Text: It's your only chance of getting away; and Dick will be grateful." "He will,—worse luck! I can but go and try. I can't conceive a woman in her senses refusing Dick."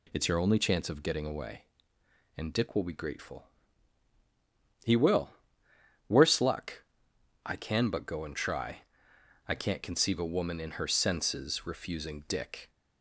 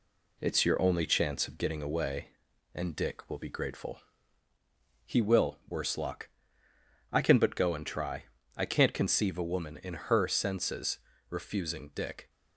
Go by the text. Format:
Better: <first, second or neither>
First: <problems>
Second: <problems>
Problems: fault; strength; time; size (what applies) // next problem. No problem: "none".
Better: first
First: none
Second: gets quieter; slight; throughout; 3 dB // pauses between "senses" and "refusing"; slight; at 10.9 s; 0.28 s long